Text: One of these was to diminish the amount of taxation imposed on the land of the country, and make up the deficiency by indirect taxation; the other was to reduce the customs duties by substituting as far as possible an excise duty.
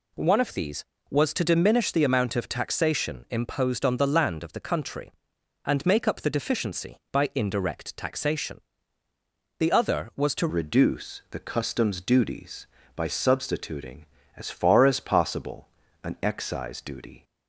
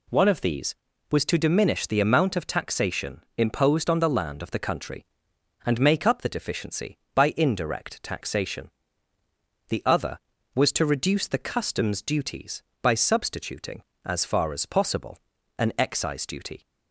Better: second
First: changes voice at "reduce"; from 10.4 s on; 6.8 s long // pauses between "possible" and "an"; slight; at 15.6 s; 0.36 s long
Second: pauses between "possible" and "an"; at 15.1 s; 0.40 s long

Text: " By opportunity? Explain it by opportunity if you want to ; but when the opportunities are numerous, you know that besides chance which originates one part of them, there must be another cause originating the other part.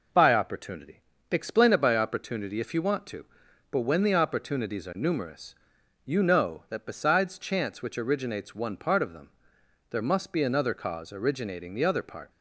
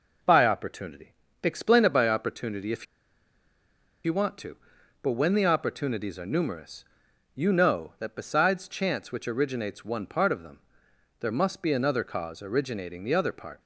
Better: first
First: none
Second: pauses between "if" and "you"; at 2.8 s; 1.2 s long

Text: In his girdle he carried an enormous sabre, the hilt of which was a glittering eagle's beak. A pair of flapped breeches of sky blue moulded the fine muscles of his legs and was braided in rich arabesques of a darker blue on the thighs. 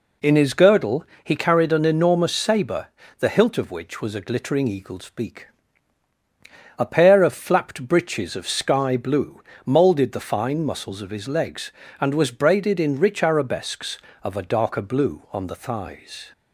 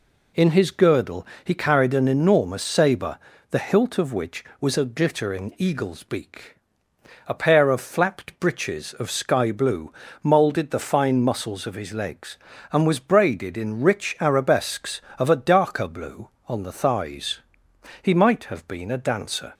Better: first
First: pauses between "girdle" and "he"; slight; at 1.0 s; 0.18 s long // pauses between "blue" and "moulded"; slight; at 9.3 s; 0.24 s long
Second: pauses between "girdle" and "he"; slight; at 1.2 s; 0.18 s long // pauses between "blue" and "moulded"; slight; at 9.9 s; 0.30 s long // goes on to say "He might have been a dancer"; from 18.0 s on; 1.5 s long

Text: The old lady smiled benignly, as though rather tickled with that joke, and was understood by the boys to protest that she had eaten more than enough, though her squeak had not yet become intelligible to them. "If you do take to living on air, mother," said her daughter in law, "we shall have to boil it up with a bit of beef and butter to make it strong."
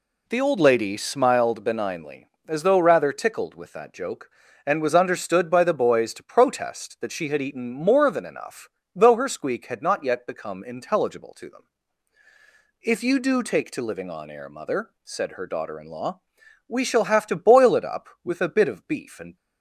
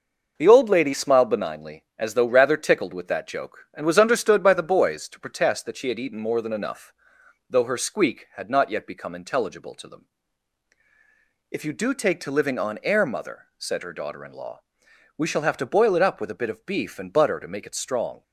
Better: second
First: stops before "butter to make it strong"; at 19.3 s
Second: none

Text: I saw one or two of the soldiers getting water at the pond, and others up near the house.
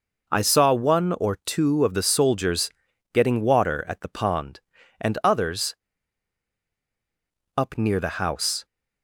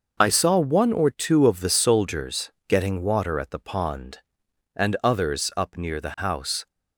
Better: second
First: pauses between "soldiers" and "getting"; at 2.6 s; 0.44 s long // pauses between "others" and "up"; strong; at 5.7 s; 1.8 s long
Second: pauses between "soldiers" and "getting"; slight; at 2.4 s; 0.18 s long

